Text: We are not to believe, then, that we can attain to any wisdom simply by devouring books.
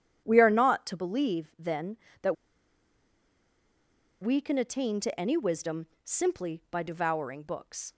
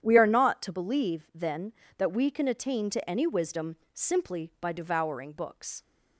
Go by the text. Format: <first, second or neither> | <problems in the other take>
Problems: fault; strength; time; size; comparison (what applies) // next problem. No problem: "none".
second | starts louder than the rest; strong; until 1.2 s; 9.5 dB; strong in the second // pauses between "that" and "we"; strong; at 2.3 s; 1.8 s long // pauses between "wisdom" and "simply"; slight; at 5.8 s; 0.16 s long; slight in the second